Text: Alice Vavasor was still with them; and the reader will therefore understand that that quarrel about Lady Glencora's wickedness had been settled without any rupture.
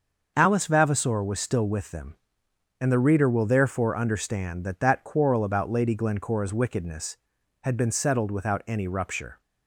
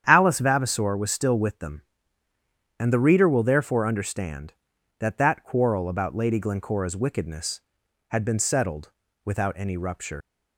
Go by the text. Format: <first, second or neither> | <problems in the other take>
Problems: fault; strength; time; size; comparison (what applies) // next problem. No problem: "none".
first | starts louder than the rest; strong; until 1.0 s; 9 dB; also in the first // pauses between "settled" and "without"; slight; at 8.9 s; 0.34 s long // leaves "rupture" unfinished; at 10.2 s; 105 ms